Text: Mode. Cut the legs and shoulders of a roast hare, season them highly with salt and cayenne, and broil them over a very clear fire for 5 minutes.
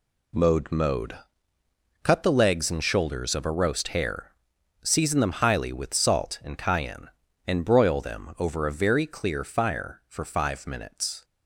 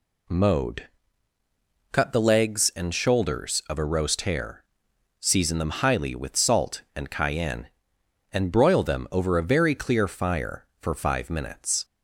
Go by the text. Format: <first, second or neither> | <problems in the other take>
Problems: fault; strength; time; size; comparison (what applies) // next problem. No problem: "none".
second | says "Mode" twice; at 0.7 s